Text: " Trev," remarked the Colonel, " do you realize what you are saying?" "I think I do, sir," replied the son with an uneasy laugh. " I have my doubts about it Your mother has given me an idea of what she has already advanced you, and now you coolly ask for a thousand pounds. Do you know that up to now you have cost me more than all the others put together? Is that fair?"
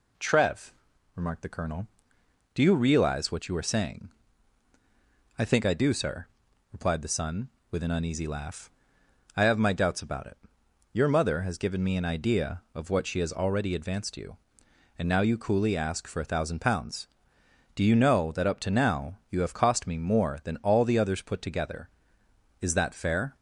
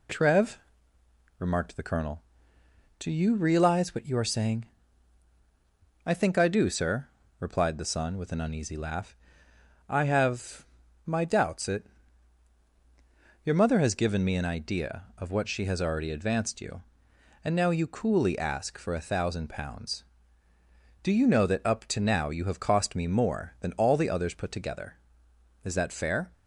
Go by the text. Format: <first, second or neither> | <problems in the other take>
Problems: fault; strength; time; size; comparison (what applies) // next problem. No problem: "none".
first | pauses between "have" and "my"; at 10.6 s; 0.38 s long // skips "about"; at 11.6 s // pauses between "it" and "Your"; strong; at 11.8 s; 1.5 s long; noticeable in the first